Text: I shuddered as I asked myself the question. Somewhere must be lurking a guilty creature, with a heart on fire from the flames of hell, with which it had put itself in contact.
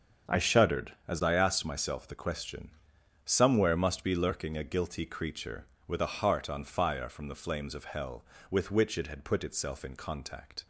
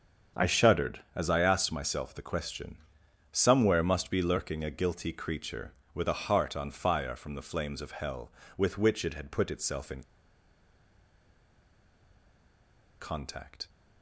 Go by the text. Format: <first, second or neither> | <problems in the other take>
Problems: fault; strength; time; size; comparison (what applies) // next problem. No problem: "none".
first | starts louder than the rest; strong; until 1.5 s; 7.5 dB; strong in the first // pauses between "in" and "contact"; strong; at 10.0 s; 2.9 s long